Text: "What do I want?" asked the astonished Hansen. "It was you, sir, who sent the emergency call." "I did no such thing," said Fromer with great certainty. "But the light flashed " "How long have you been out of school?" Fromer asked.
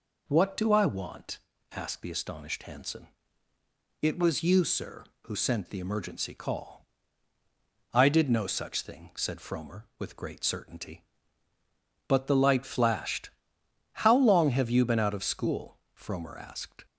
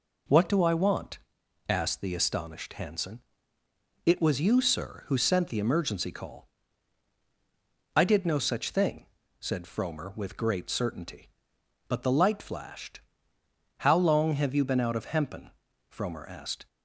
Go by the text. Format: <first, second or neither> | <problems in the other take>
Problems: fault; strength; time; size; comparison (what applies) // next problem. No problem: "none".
first | says "hempen" for "school"; at 15.0 s